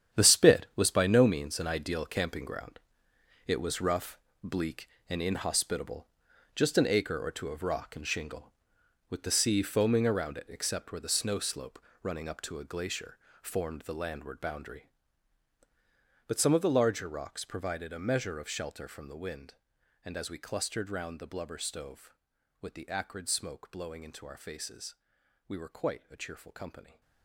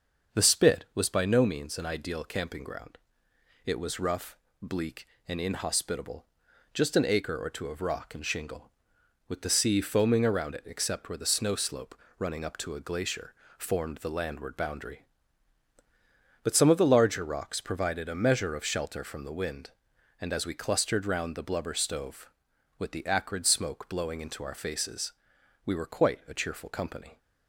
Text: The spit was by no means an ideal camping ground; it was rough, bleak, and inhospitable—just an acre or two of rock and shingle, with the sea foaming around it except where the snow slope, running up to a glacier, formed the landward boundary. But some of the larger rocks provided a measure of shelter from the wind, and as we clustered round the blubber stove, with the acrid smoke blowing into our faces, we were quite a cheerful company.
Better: second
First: gets quieter; strong; throughout; 12 dB // starts louder than the rest; strong; until 1.2 s; 9.5 dB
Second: starts louder than the rest; until 1.4 s; 6.5 dB

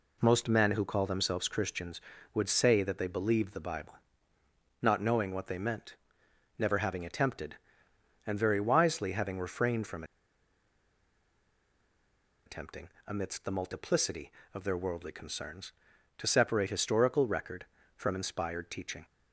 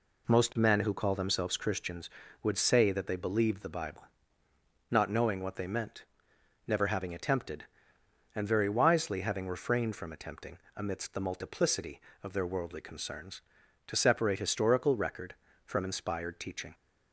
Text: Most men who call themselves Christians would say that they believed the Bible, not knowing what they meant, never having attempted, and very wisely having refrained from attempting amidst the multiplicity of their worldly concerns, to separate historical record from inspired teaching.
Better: second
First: pauses between "from" and "attempting"; strong; at 10.0 s; 2.4 s long // pauses between "attempting" and "amidst"; slight; at 12.8 s; 0.18 s long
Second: pauses between "attempting" and "amidst"; slight; at 10.5 s; 0.18 s long

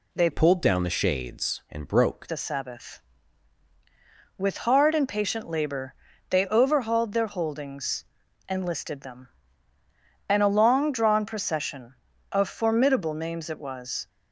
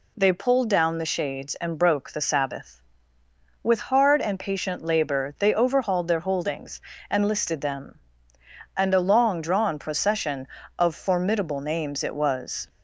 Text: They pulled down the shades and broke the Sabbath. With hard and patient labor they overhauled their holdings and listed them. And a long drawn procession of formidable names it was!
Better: second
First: changes voice from "pulled" to "broke"; from 0.3 to 2.2 s; 1.9 s long // pauses between "labor" and "they"; slight; at 5.9 s; 0.34 s long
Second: none

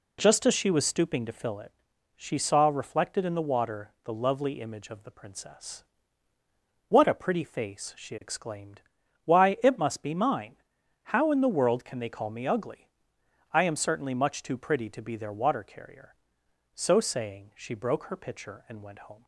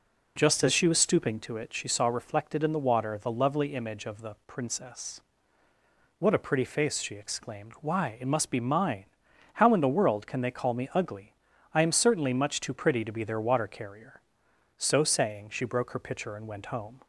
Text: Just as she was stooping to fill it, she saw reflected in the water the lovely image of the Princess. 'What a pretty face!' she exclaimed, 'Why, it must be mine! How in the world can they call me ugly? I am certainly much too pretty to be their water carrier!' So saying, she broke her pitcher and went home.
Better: first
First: none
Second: skips "fill"; at 1.5 s

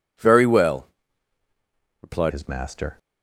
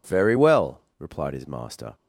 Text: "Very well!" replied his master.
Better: second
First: changes voice at "his"; from 2.3 s on; 0.6 s long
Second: none

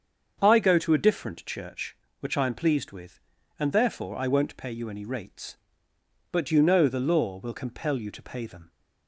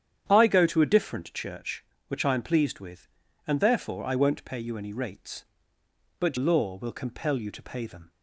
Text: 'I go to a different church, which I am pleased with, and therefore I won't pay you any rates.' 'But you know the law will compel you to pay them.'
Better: first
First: starts louder than the rest; strong; until 1.4 s; 7 dB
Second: starts louder than the rest; strong; until 1.2 s; 9.5 dB // skips "you know the"; at 6.3 s

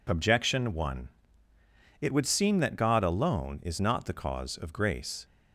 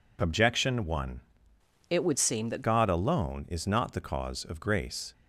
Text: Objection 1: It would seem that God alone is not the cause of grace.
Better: first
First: none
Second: changes voice from "It" to "that"; from 1.9 to 2.6 s; 0.7 s long

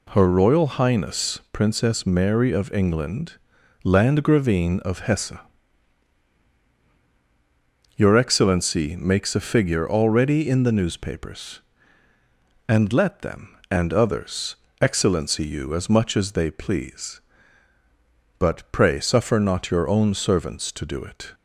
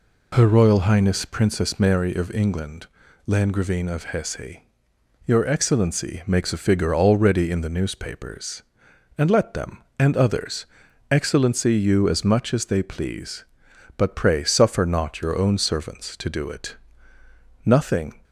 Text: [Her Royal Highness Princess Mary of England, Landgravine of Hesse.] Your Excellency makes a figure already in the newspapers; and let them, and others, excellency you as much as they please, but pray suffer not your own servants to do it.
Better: first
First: none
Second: goes on to say "Nothing"; from 17.6 s on; 0.52 s long

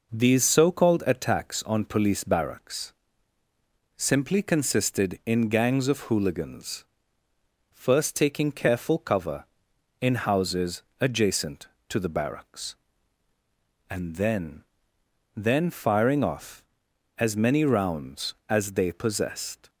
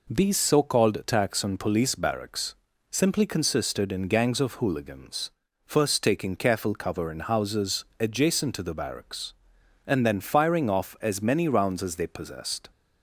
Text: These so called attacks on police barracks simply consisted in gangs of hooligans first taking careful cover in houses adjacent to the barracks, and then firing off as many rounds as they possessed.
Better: second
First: pauses between "barracks" and "simply"; at 2.9 s; 1.0 s long // pauses between "hooligans" and "first"; noticeable; at 6.8 s; 0.88 s long // pauses between "houses" and "adjacent"; slight; at 10.8 s; 0.18 s long // says "then" twice; at 15.3 s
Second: pauses between "barracks" and "simply"; slight; at 2.5 s; 0.36 s long // pauses between "hooligans" and "first"; slight; at 5.3 s; 0.36 s long // pauses between "houses" and "adjacent"; slight; at 7.8 s; 0.16 s long

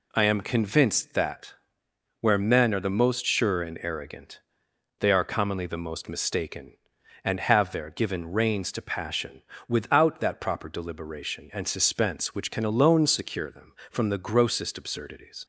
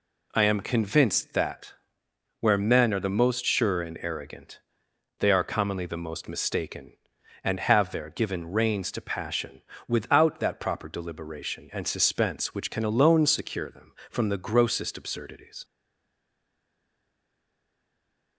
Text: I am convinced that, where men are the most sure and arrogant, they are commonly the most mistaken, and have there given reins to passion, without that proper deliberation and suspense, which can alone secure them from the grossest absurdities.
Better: first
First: none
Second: stays silent after the last word; strong; from 15.6 s on; 2.7 s long

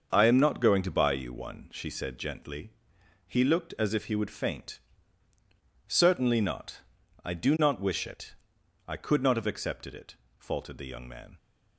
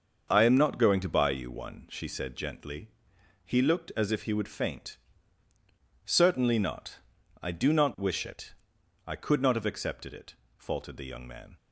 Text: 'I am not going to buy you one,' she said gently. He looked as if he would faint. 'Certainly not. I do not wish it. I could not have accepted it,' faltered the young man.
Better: neither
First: starts louder than the rest; until 1.1 s; 6.5 dB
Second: starts louder than the rest; until 1.3 s; 6.5 dB

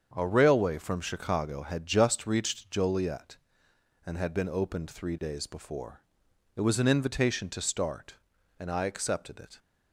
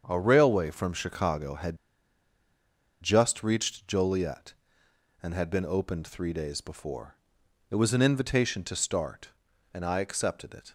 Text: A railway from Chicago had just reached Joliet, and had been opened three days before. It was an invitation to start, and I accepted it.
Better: first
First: starts louder than the rest; strong; until 1.1 s; 7 dB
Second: starts louder than the rest; strong; until 1.0 s; 7 dB // pauses between "had" and "just"; strong; at 1.7 s; 1.2 s long

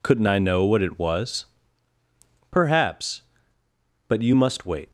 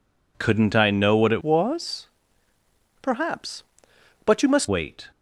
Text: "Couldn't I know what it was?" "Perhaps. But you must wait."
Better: first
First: none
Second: changes voice from "was" to "must"; from 1.4 to 4.6 s; 3.2 s long

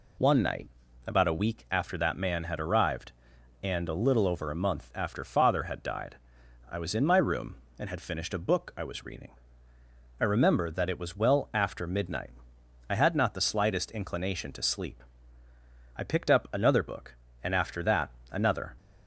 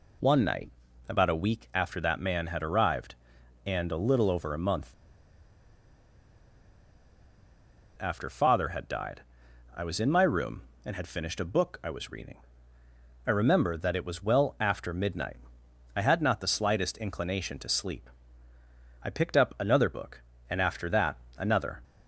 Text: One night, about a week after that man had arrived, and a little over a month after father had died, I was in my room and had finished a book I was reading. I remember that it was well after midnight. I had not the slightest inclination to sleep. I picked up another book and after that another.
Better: first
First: pauses between "that" and "another"; slight; at 18.0 s; 0.22 s long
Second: pauses between "month" and "after"; strong; at 4.9 s; 3.0 s long // pauses between "that" and "another"; slight; at 21.1 s; 0.22 s long

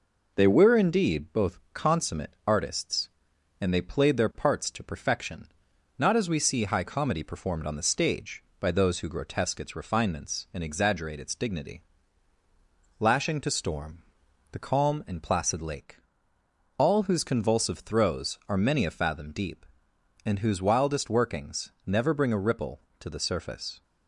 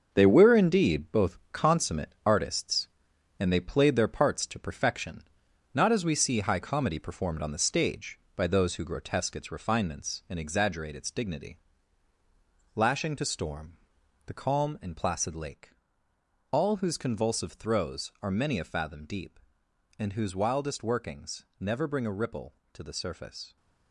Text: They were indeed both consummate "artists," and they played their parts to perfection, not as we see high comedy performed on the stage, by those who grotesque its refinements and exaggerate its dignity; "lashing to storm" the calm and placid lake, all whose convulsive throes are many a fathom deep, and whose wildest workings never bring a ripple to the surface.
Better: first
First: pauses between "storm" and "the"; noticeable; at 14.0 s; 0.50 s long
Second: gets quieter; strong; throughout; 8.5 dB // pauses between "storm" and "the"; noticeable; at 13.7 s; 0.50 s long

